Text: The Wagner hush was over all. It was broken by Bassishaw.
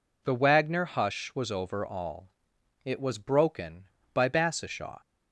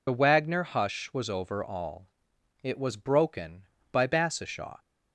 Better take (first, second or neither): first